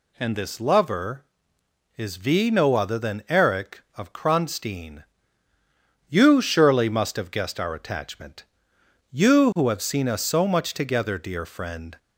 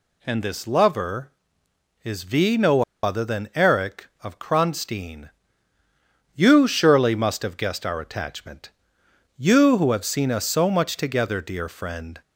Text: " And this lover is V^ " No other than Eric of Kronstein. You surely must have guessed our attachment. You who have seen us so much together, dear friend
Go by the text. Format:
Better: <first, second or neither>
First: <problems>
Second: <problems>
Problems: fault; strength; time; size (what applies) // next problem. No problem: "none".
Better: first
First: none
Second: pauses between "No" and "other"; slight; at 2.8 s; 0.21 s long